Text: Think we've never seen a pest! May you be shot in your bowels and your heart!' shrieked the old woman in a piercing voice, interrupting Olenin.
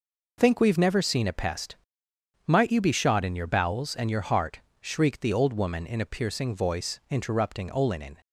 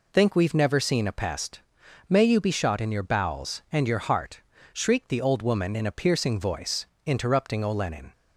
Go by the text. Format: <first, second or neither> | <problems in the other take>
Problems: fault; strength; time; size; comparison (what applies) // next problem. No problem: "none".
second | says "Might" for "May"; at 2.4 s